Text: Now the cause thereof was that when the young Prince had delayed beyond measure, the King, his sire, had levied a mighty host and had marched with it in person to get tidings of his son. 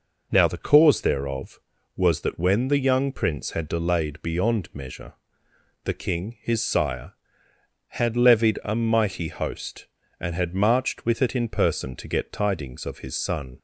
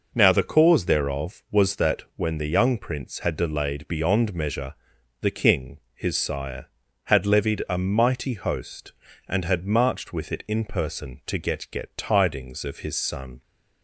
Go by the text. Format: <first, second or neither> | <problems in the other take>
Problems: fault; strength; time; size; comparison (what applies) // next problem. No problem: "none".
first | says "get" twice; at 11.6 s